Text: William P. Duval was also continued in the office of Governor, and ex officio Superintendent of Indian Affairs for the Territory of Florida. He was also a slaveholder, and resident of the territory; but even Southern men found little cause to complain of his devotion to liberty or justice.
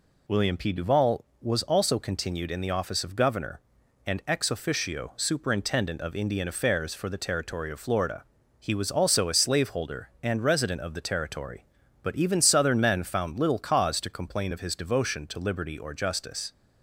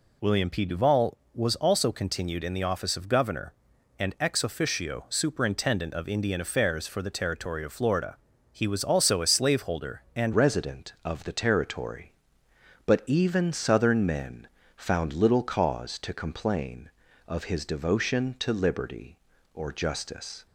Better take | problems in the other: first | changes voice at "resident"; from 10.3 s on; 10.1 s long // pauses between "men" and "found"; slight; at 14.4 s; 0.28 s long

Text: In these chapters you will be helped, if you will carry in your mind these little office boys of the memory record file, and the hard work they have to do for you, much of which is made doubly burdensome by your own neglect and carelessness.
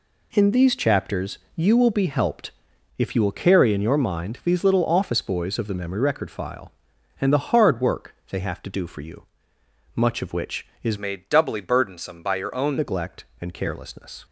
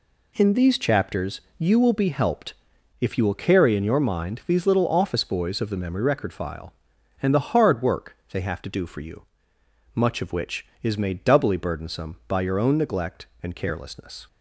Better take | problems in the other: second | pauses between "chapters" and "you"; slight; at 1.3 s; 0.18 s long; slight in the second // pauses between "work" and "they"; slight; at 8.1 s; 0.16 s long; slight in the second // changes voice from "made" to "own"; from 10.9 to 12.7 s; 1.8 s long

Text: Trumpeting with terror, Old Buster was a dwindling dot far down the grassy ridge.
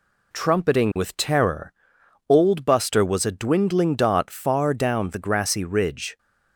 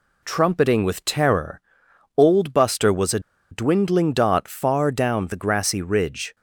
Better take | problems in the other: first | pauses between "a" and "dwindling"; slight; at 3.1 s; 0.31 s long

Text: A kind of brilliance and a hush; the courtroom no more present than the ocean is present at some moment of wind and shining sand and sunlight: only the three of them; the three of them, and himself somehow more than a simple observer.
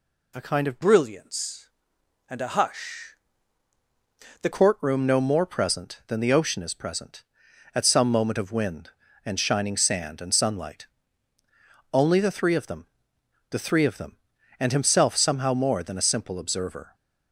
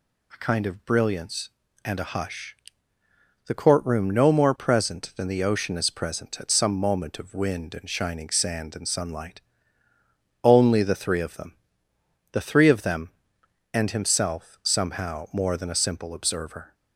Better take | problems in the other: second | changes voice from "brilliance" to "the"; from 0.8 to 4.4 s; 3.6 s long

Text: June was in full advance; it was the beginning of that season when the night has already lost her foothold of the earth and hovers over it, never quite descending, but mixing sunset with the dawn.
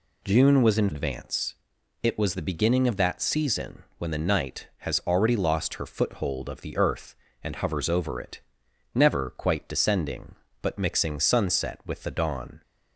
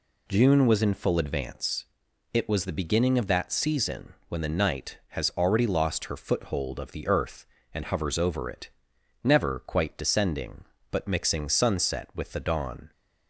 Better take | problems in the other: second | skips "full"; at 0.9 s

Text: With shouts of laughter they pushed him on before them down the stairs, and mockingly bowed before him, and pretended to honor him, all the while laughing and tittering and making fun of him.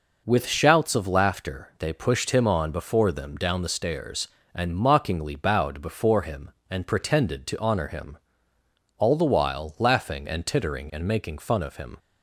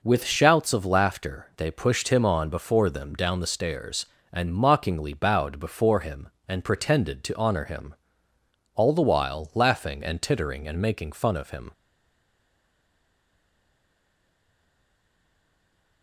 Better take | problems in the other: first | stays silent after the last word; strong; from 11.7 s on; 4.3 s long

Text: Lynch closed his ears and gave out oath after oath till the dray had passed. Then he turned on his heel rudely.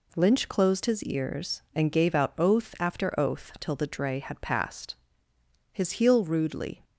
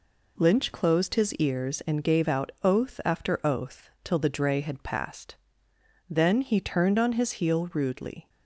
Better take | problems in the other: second | skips "Then he turned on"; at 5.3 s

